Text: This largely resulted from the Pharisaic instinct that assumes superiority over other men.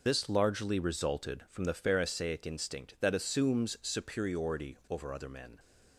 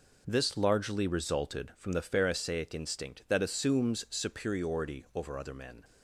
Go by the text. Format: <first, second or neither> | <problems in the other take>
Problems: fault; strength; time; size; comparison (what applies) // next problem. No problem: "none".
second | loses the start of "This"; at 0.0 s; 70 ms